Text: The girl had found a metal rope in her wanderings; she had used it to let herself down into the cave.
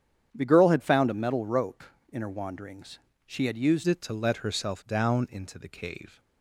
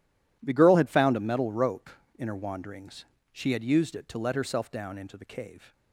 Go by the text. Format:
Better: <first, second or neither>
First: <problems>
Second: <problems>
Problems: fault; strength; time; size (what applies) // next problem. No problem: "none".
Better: second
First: starts louder than the rest; strong; until 1.3 s; 9 dB // changes voice at "it"; from 3.8 s on; 2.3 s long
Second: none